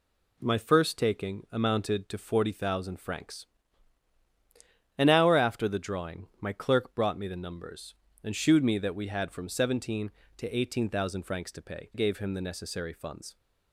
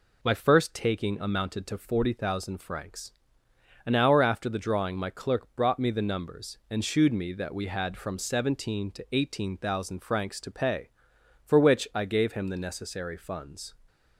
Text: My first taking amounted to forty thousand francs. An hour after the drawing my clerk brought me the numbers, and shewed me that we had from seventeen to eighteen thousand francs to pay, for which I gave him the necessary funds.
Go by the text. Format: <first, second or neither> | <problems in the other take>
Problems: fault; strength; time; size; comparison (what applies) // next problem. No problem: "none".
second | skips "for which I"; at 11.9 s